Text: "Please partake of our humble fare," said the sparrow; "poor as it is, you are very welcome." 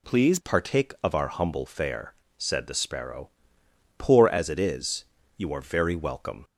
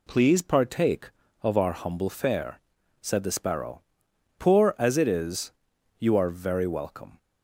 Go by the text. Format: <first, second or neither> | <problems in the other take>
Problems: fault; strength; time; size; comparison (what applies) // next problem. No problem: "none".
second | changes voice at "partake"; from 0.4 s on; 6.0 s long